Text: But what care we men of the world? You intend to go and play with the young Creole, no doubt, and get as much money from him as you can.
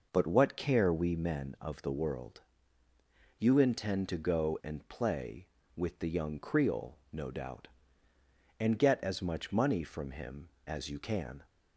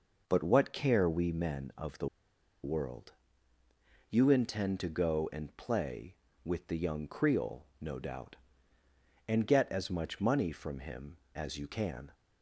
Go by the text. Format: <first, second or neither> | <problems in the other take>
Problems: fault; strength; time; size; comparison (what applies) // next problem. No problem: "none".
first | pauses between "the" and "world"; noticeable; at 2.0 s; 0.56 s long